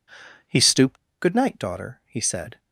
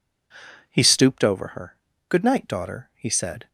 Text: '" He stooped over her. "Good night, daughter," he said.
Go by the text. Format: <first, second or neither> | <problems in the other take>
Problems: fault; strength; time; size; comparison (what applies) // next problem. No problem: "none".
second | skips "over her"; at 1.0 s